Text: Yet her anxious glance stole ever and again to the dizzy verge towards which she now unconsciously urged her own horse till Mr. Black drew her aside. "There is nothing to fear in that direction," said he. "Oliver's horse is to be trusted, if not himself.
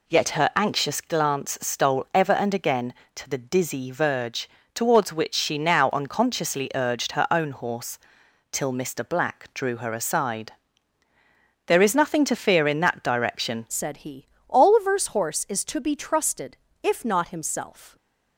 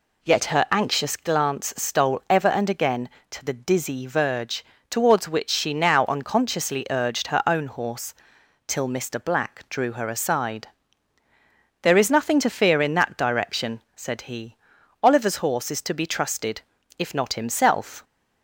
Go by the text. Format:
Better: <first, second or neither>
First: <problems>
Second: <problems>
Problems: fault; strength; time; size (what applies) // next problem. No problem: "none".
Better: second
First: pauses between "verge" and "towards"; slight; at 4.4 s; 0.26 s long // pauses between "horse" and "till"; noticeable; at 7.9 s; 0.54 s long // changes voice at "said"; from 13.6 s on; 4.3 s long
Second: pauses between "verge" and "towards"; slight; at 4.6 s; 0.26 s long // pauses between "horse" and "till"; noticeable; at 8.1 s; 0.54 s long